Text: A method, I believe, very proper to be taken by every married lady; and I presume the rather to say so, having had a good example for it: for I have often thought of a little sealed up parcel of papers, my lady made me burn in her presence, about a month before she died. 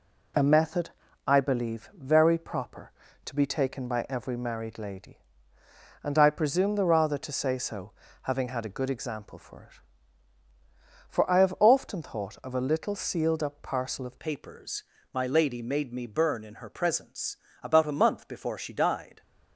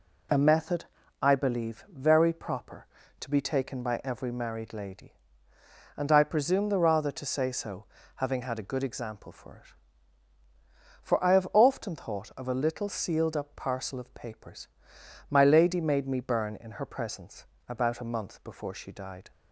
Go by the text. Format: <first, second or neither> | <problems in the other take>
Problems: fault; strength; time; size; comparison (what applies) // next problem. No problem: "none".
second | changes voice at "papers"; from 14.1 s on; 5.1 s long